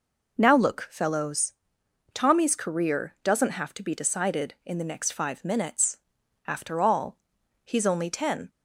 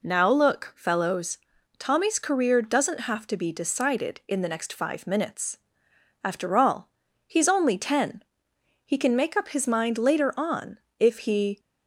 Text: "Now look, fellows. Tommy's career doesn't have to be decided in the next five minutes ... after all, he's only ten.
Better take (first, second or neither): first